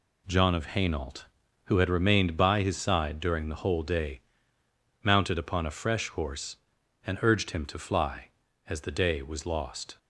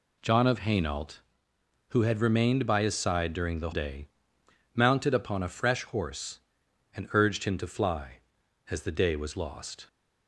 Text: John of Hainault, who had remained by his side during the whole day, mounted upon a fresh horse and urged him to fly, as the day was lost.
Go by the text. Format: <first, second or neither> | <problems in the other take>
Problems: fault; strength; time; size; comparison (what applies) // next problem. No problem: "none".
first | skips "whole"; at 3.7 s